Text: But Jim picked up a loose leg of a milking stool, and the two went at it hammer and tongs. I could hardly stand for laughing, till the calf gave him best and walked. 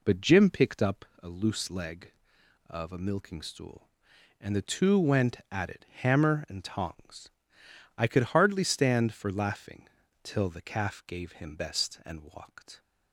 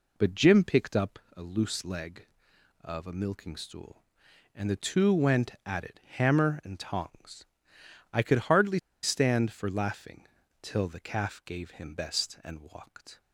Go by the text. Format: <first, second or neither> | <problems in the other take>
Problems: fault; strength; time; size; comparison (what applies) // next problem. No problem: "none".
first | pauses between "up" and "a"; slight; at 1.1 s; 0.18 s long; slight in the first // pauses between "hardly" and "stand"; slight; at 8.7 s; 0.25 s long